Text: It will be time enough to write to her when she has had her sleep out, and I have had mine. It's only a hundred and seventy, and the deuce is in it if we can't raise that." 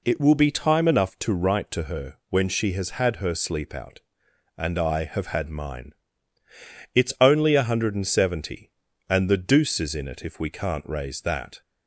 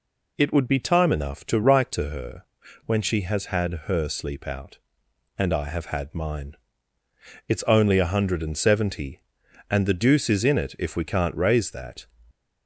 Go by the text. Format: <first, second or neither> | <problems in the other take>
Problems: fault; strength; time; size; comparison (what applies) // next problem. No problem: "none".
first | says "would" for "will"; at 0.5 s // pauses between "her" and "when"; at 2.4 s; 0.42 s long